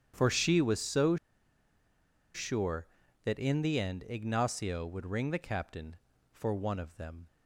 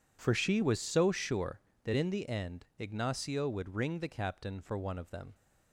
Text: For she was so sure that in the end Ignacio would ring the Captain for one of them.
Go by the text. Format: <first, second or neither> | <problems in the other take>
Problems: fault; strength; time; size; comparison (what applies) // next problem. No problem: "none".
second | starts louder than the rest; strong; until 1.1 s; 9 dB // pauses between "so" and "sure"; at 1.1 s; 1.1 s long